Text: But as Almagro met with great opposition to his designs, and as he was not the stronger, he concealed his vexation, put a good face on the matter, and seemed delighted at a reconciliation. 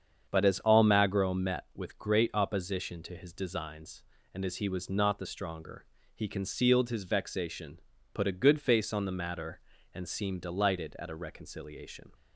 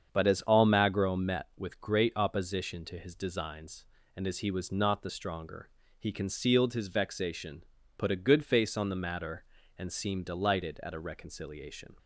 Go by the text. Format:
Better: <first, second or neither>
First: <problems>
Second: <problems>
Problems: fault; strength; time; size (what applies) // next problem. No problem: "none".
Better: neither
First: starts louder than the rest; strong; until 1.3 s; 7.5 dB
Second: starts louder than the rest; strong; until 1.1 s; 7.5 dB